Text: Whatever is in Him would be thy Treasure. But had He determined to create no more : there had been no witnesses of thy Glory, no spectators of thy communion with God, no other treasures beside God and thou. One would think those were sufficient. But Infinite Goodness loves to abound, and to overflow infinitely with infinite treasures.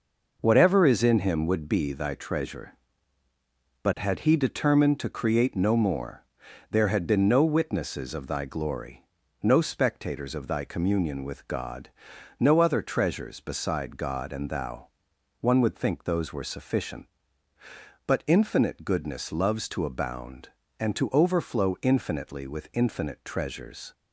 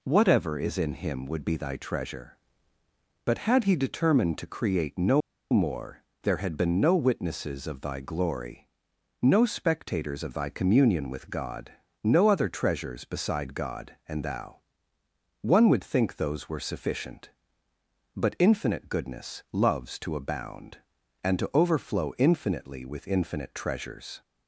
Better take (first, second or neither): first